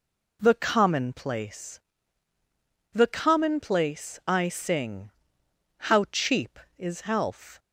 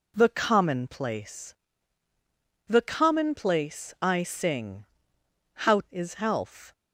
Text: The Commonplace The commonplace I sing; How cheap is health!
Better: first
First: pauses between "Commonplace" and "The"; at 1.8 s; 1.1 s long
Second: pauses between "Commonplace" and "The"; at 1.5 s; 1.1 s long // skips "cheap"; at 5.8 s

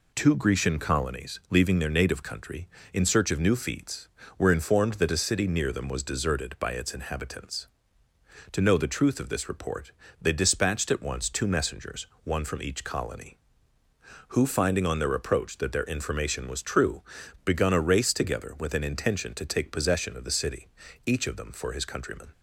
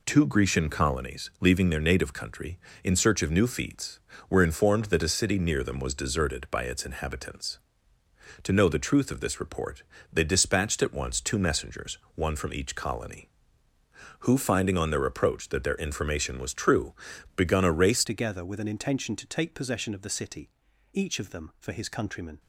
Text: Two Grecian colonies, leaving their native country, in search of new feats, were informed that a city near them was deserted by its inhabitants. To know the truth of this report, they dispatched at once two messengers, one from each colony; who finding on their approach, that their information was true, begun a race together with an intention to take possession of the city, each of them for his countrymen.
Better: first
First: none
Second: changes voice at "together"; from 18.0 s on; 4.3 s long

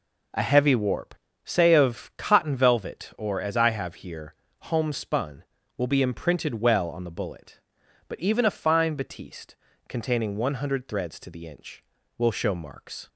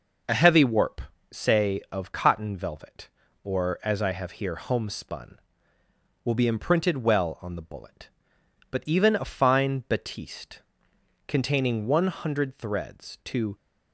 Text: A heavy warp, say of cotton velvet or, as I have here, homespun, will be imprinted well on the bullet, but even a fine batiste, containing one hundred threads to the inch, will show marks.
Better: first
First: none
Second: stops before "the inch will show marks"; at 13.5 s

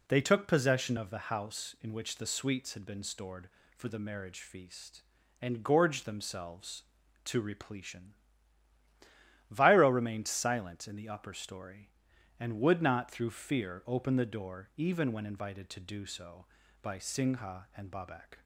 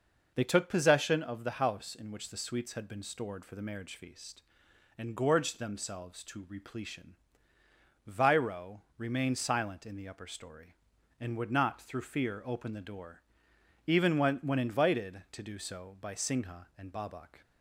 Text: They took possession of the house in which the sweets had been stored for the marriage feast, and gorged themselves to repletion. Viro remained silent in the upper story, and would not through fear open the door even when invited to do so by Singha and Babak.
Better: first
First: none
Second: pauses between "Viro" and "remained"; slight; at 8.8 s; 0.16 s long // pauses between "door" and "even"; noticeable; at 13.2 s; 0.66 s long // says "when" twice; at 14.4 s

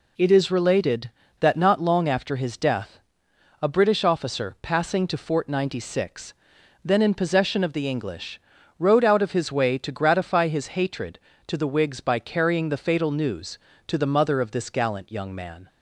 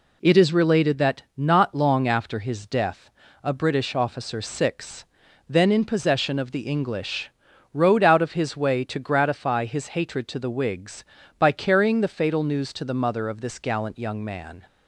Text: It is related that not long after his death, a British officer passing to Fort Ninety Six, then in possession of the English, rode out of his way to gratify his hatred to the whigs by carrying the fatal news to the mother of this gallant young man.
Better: first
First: none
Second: skips "passing to Fort Ninety"; at 4.4 s

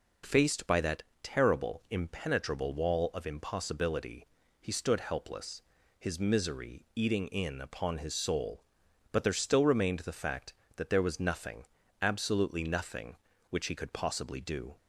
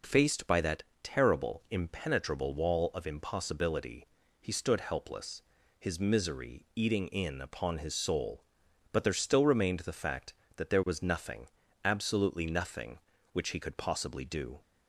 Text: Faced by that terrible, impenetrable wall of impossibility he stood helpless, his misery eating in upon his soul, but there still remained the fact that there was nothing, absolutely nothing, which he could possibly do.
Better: neither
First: pauses between "that" and "terrible"; slight; at 1.0 s; 0.20 s long // pauses between "impossibility" and "he"; slight; at 4.2 s; 0.34 s long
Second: pauses between "that" and "terrible"; slight; at 0.8 s; 0.20 s long // pauses between "impossibility" and "he"; slight; at 4.0 s; 0.34 s long

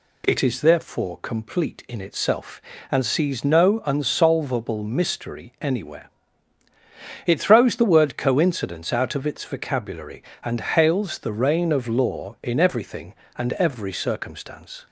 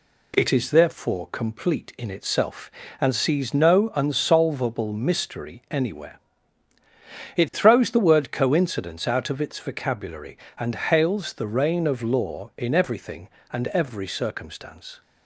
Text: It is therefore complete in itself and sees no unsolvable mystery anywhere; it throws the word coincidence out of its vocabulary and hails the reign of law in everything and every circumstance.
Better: first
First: none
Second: gets quieter; noticeable; throughout; 4 dB

